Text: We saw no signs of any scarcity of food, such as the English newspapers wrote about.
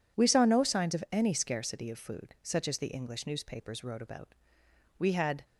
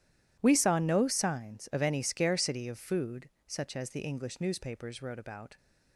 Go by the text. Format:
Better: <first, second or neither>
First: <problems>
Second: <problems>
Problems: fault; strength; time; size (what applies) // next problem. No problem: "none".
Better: second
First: goes on to say "We had"; slight; from 4.9 s on; 0.46 s long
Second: none